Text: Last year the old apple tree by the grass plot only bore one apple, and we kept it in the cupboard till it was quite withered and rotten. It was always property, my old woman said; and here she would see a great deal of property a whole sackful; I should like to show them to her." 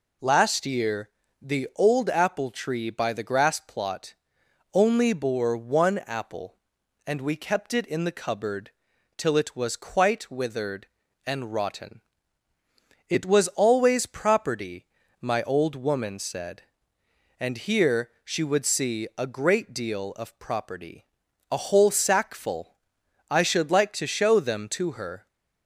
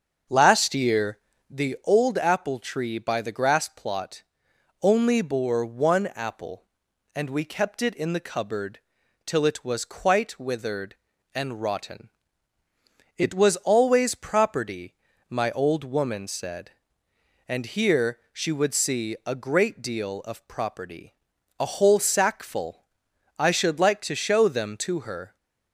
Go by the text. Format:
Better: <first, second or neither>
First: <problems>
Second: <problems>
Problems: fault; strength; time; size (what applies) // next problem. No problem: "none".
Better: first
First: pauses between "year" and "the"; slight; at 1.0 s; 0.32 s long // pauses between "plot" and "only"; noticeable; at 4.1 s; 0.58 s long // pauses between "cupboard" and "till"; noticeable; at 8.7 s; 0.46 s long // pauses between "property" and "a"; noticeable; at 21.0 s; 0.46 s long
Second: starts louder than the rest; until 1.6 s; 7 dB // pauses between "year" and "the"; slight; at 1.1 s; 0.32 s long // pauses between "plot" and "only"; noticeable; at 4.2 s; 0.58 s long // pauses between "cupboard" and "till"; noticeable; at 8.7 s; 0.46 s long // pauses between "property" and "a"; noticeable; at 21.1 s; 0.46 s long